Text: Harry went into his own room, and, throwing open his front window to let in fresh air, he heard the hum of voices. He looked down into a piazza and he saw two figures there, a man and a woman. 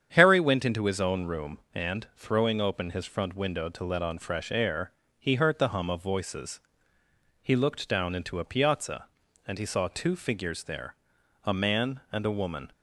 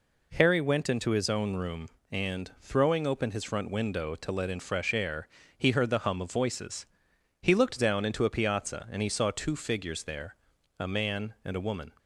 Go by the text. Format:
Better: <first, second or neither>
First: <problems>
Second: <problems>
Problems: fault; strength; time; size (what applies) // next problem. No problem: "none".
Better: second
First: starts louder than the rest; strong; until 1.1 s; 8.5 dB // says "on" for "in"; at 4.0 s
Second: none